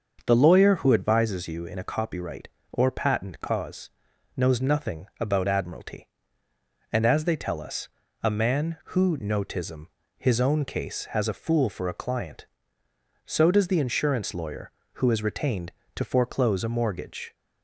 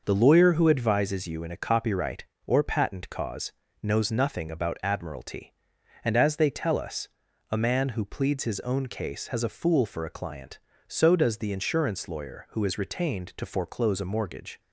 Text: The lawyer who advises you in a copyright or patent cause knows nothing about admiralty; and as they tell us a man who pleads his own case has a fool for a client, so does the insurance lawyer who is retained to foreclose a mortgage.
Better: second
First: starts louder than the rest; until 1.2 s; 6.5 dB // pauses between "cause" and "knows"; noticeable; at 3.8 s; 0.46 s long // pauses between "us" and "a"; slight; at 7.8 s; 0.34 s long // says "notism" for "pleads"; at 9.1 s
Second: starts louder than the rest; noticeable; until 1.0 s; 6 dB // pauses between "cause" and "knows"; slight; at 3.5 s; 0.32 s long // pauses between "us" and "a"; at 7.0 s; 0.44 s long

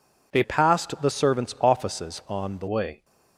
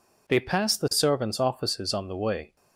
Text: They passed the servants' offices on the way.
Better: second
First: changes voice from "passed" to "the"; from 0.4 to 2.6 s; 2.2 s long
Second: none

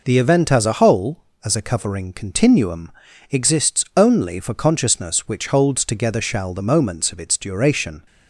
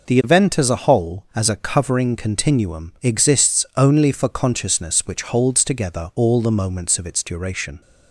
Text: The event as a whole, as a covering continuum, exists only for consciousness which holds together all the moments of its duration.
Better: second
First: says "shall" for "all"; at 6.2 s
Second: none

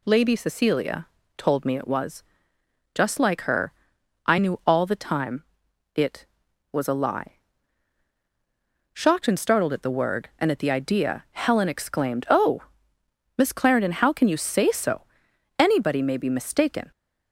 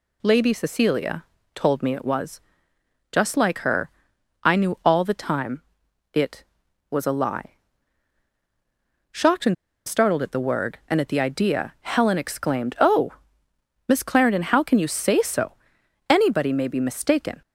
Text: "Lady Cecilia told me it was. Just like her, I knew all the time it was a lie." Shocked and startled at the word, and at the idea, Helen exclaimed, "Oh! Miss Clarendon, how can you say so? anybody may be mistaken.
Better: first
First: pauses between "Cecilia" and "told"; slight; at 1.0 s; 0.30 s long // pauses between "time" and "it"; noticeable; at 5.4 s; 0.50 s long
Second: pauses between "Cecilia" and "told"; slight; at 1.2 s; 0.30 s long // pauses between "time" and "it"; noticeable; at 5.6 s; 0.50 s long // pauses between "and" and "startled"; slight; at 9.5 s; 0.32 s long

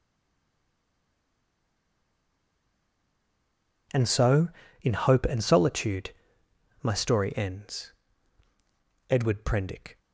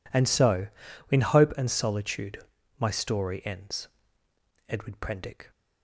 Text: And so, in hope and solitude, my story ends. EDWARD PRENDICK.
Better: second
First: stays silent before the first word; strong; until 3.9 s; 3.9 s long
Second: none

